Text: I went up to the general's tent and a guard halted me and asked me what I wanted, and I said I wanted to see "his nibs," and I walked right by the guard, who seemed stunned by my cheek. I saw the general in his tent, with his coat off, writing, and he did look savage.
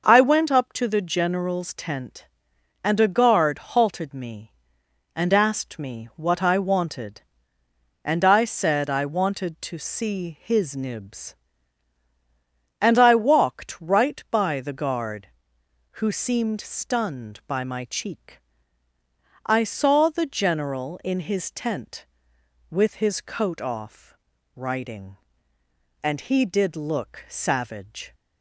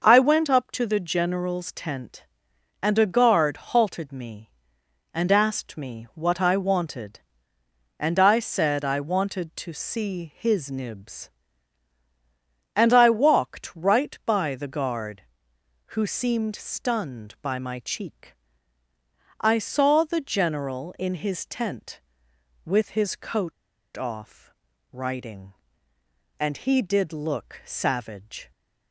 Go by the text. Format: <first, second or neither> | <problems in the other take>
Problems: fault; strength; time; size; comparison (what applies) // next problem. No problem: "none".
first | pauses between "coat" and "off"; at 23.5 s; 0.44 s long